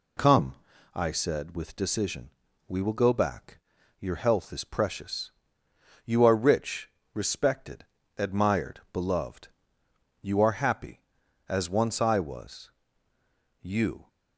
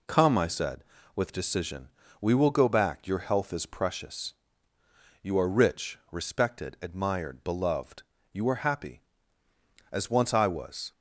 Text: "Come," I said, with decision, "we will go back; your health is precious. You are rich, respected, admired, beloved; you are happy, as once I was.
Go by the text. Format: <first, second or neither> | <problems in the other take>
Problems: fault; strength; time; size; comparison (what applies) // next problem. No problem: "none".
second | goes on to say "You"; slight; from 13.6 s on; 0.46 s long